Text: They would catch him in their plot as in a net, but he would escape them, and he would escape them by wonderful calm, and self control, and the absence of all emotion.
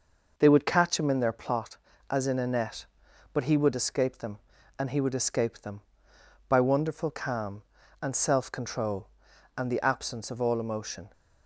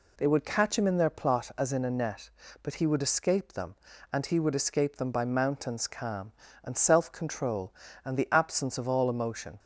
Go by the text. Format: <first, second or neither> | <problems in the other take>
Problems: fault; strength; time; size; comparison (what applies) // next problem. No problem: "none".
first | says "mountains" for "wonderful"; at 5.2 s